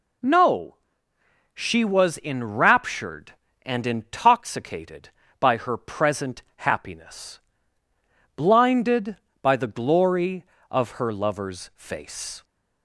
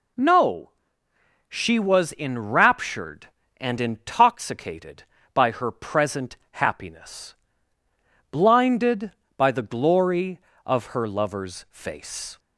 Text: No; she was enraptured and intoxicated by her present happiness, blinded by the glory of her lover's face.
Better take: neither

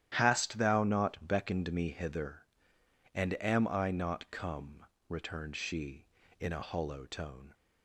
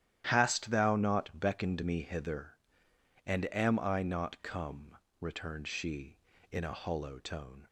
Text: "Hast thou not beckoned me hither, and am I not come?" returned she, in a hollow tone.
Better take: neither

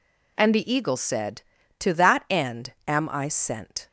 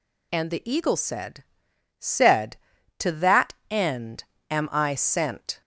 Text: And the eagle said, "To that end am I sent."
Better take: first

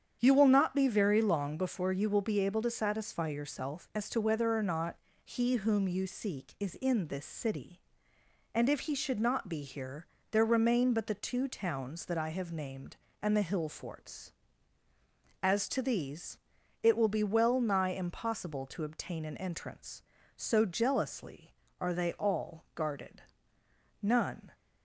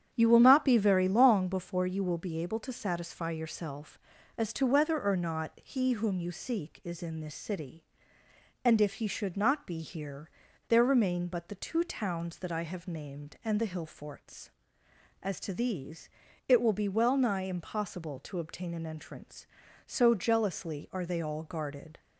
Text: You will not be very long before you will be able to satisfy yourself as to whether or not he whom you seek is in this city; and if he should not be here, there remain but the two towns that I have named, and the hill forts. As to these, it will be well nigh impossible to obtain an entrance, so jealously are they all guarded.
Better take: second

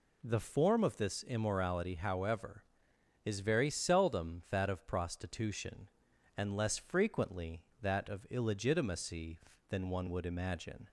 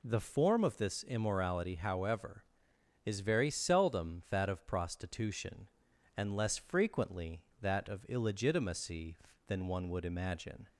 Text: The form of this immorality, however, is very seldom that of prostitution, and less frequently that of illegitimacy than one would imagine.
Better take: neither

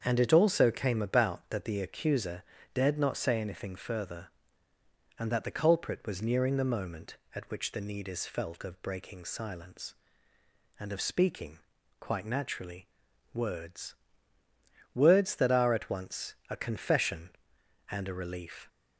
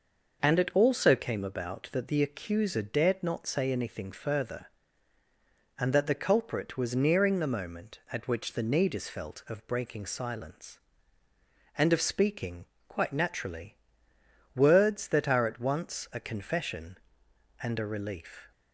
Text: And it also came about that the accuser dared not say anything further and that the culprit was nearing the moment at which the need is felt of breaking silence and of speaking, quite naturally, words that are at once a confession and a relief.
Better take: second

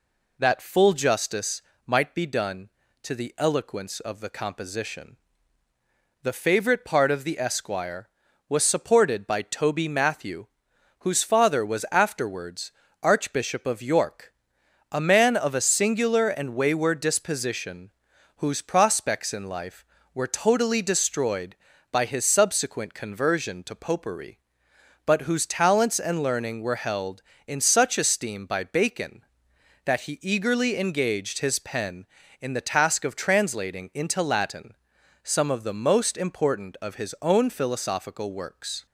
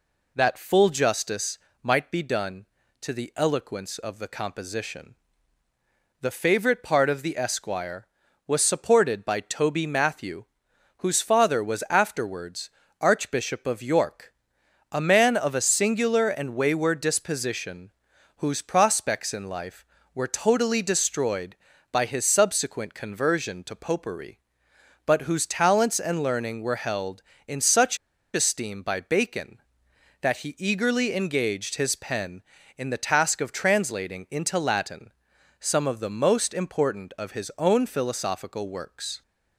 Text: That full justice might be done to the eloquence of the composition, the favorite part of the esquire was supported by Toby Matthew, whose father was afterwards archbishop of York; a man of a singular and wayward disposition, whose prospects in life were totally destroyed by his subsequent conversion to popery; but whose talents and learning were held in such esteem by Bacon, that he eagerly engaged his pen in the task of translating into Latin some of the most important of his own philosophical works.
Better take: first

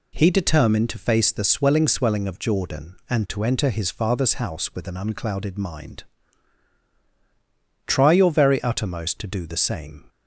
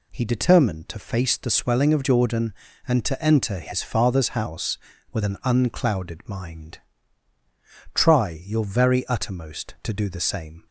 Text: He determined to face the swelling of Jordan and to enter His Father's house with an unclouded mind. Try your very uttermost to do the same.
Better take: second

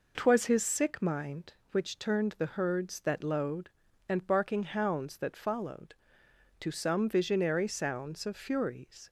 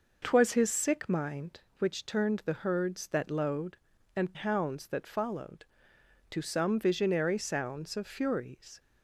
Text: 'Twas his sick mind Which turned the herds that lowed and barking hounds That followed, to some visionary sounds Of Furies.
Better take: first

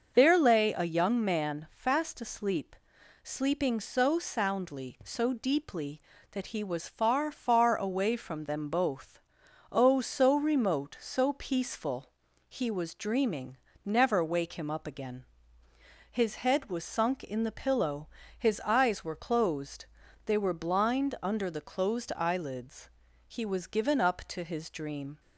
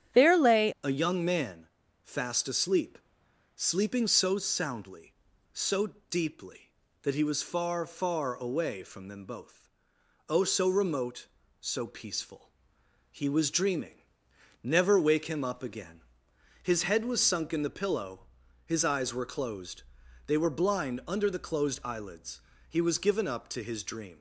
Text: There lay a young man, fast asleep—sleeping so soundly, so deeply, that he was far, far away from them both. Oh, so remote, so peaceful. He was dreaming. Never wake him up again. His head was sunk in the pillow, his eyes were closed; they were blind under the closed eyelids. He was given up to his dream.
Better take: first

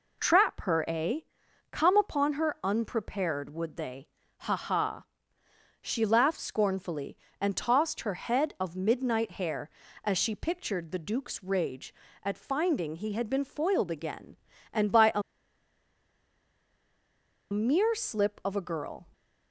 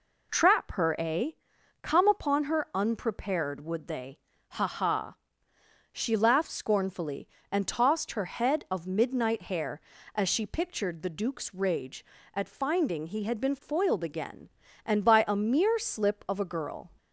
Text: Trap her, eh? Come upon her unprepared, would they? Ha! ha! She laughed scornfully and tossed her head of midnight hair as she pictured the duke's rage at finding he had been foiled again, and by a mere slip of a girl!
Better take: second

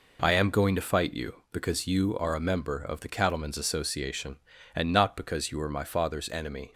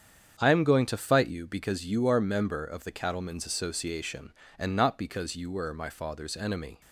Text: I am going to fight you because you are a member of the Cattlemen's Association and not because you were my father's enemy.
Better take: first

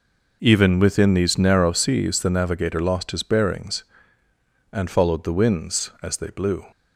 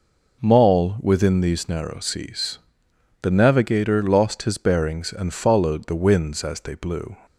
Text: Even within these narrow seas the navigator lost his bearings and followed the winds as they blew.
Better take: first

